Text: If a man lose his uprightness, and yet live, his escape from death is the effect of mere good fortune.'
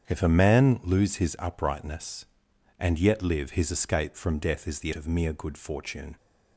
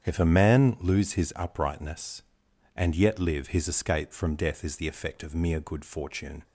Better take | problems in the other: second | starts louder than the rest; strong; until 1.0 s; 8 dB; strong in the second // skips "effect"; at 4.9 s

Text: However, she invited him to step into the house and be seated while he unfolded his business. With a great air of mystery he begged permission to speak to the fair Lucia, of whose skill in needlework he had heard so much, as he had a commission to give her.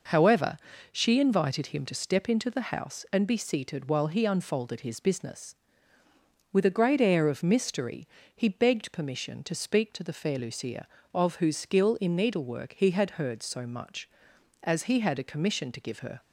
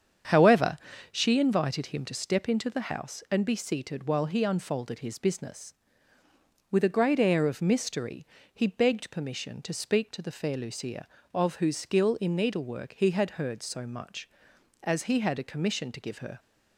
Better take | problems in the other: first | starts louder than the rest; strong; until 1.3 s; 8 dB // pauses between "mystery" and "he"; slight; at 8.2 s; 0.26 s long; slight in the first

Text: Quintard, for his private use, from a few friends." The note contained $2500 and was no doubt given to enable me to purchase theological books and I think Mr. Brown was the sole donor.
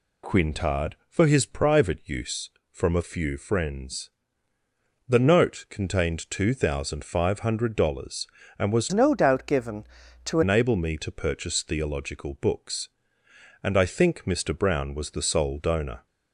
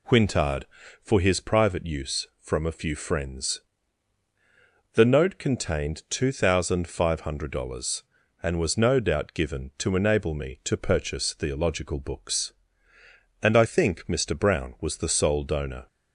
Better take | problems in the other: second | changes voice from "no" to "to"; from 8.9 to 10.4 s; 1.5 s long

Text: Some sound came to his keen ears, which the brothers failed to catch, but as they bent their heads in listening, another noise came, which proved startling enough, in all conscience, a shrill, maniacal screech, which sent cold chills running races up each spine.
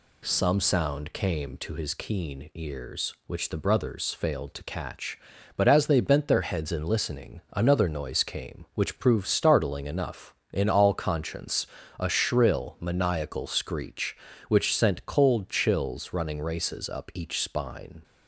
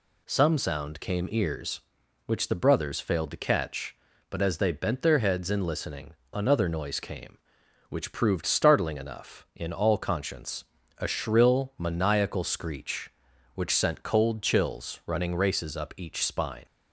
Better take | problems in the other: first | skips "to his keen"; at 1.2 s

